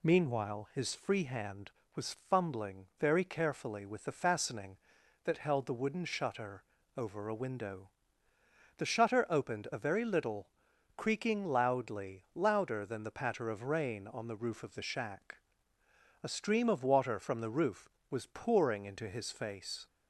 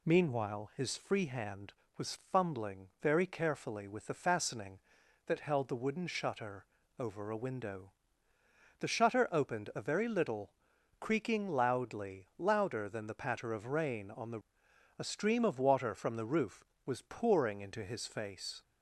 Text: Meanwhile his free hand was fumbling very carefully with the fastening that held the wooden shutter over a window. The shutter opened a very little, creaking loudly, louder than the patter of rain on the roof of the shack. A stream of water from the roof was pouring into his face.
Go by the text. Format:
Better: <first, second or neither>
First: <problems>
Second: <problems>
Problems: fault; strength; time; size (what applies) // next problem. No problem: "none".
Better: first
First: pauses between "shutter" and "over"; slight; at 6.6 s; 0.34 s long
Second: pauses between "shutter" and "over"; slight; at 6.6 s; 0.34 s long // skips "roof of the shack"; at 14.6 s